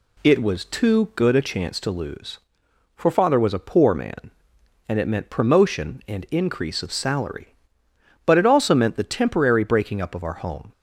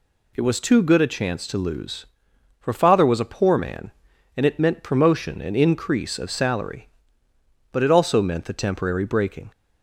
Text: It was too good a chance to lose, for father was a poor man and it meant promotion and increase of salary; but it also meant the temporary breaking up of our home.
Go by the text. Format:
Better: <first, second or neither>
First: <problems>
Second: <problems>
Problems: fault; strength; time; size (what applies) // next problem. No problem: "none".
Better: first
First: none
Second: stops before "up of our home"; at 9.5 s